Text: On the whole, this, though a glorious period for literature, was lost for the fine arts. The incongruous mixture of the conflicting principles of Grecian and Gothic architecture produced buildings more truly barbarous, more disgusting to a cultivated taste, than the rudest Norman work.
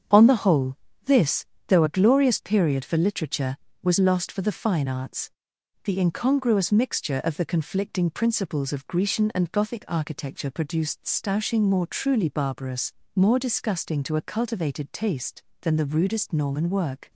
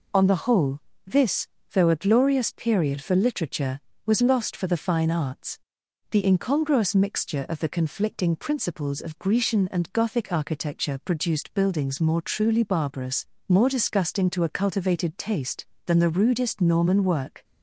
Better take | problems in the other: second | starts louder than the rest; strong; until 1.4 s; 7.5 dB // says "stoushing" for "buildings"; at 11.0 s

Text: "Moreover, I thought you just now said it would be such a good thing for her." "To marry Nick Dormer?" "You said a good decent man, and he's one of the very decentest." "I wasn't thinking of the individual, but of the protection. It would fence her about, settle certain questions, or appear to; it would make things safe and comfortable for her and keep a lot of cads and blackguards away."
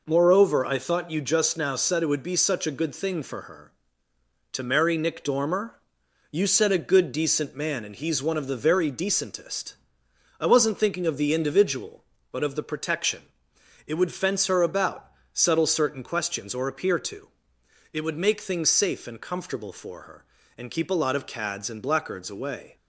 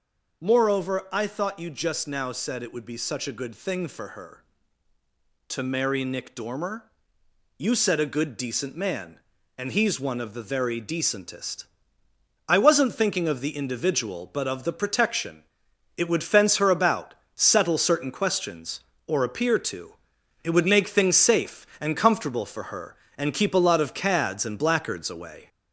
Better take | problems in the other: first | gets louder; throughout; 4 dB

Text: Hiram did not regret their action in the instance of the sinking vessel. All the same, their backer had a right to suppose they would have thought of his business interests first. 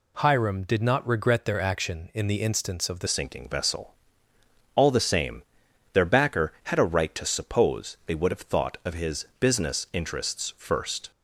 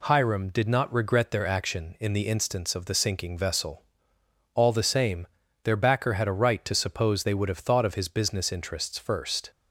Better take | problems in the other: second | changes voice at "sinking"; from 3.0 s on; 8.1 s long

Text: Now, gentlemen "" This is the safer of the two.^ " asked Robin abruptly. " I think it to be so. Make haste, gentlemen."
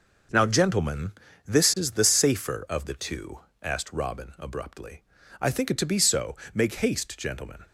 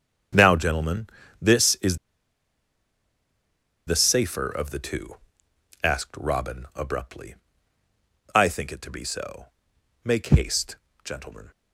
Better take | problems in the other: first | starts louder than the rest; strong; until 1.5 s; 7.5 dB // pauses between "is" and "the"; strong; at 1.9 s; 1.8 s long

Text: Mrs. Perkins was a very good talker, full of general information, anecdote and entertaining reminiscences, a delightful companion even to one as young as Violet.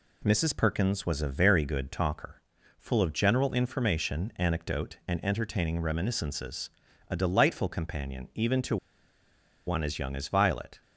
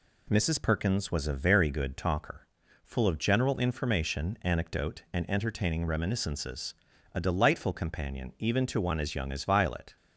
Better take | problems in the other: second | pauses between "to" and "one"; noticeable; at 8.7 s; 0.90 s long

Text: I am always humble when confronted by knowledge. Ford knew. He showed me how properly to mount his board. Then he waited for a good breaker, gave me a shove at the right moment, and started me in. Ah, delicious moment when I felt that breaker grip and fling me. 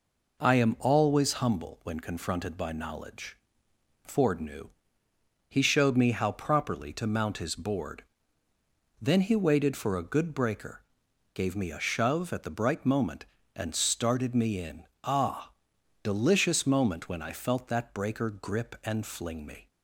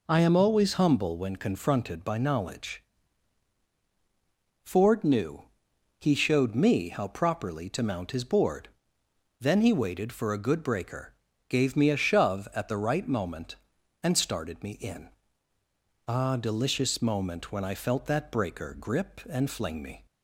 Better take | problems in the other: second | says "bright" for "right"; at 12.4 s

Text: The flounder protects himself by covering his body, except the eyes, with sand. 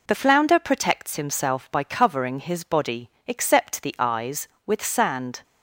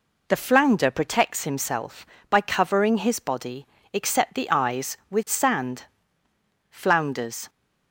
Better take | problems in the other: first | goes on to say "Flounders"; noticeable; from 6.6 s on; 0.80 s long

